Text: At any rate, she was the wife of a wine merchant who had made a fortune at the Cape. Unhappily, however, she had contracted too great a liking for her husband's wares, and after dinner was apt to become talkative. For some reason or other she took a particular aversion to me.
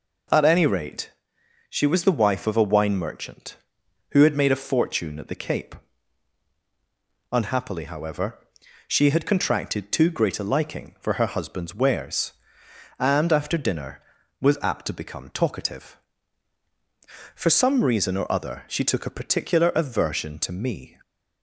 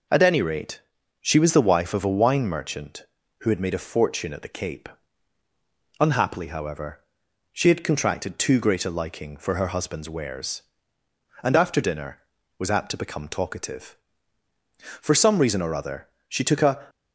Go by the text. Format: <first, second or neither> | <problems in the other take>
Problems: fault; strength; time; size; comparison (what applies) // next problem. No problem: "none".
first | pauses between "other" and "she"; slight; at 16.0 s; 0.20 s long // stops before "particular aversion to me"; at 16.8 s